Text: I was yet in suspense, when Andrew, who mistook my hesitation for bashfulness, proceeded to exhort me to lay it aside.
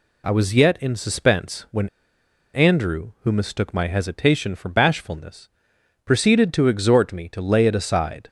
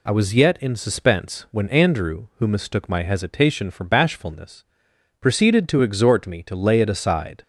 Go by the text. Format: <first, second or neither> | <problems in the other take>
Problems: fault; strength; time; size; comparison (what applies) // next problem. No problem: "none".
second | pauses between "when" and "Andrew"; noticeable; at 1.8 s; 0.66 s long